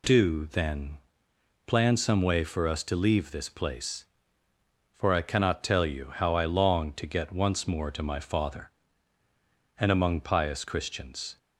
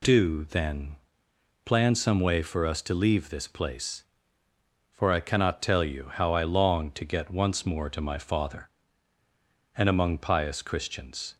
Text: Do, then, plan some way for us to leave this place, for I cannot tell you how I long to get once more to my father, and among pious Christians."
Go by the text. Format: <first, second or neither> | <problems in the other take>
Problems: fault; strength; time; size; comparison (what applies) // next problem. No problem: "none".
neither | none